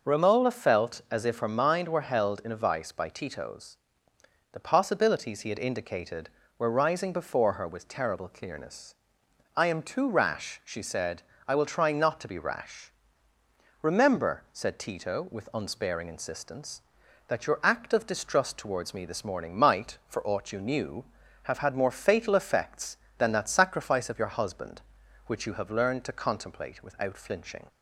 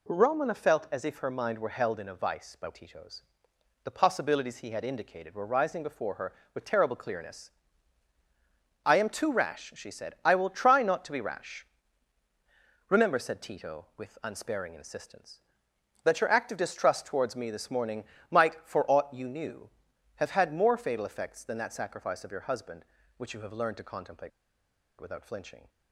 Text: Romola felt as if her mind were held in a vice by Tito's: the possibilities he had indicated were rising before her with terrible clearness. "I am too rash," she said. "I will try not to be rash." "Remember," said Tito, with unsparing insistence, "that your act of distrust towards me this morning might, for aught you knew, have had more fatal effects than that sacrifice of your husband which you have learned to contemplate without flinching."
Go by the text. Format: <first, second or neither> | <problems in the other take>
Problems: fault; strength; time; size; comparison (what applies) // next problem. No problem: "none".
first | pauses between "morning" and "might"; slight; at 18.0 s; 0.26 s long // pauses between "contemplate" and "without"; noticeable; at 24.3 s; 0.68 s long